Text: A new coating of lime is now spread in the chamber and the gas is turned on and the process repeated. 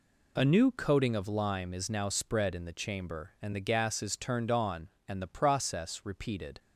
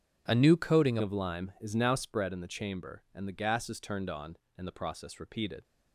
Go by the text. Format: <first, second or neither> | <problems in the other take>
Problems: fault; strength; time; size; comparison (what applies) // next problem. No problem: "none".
first | changes voice at "of"; from 1.0 s on; 4.6 s long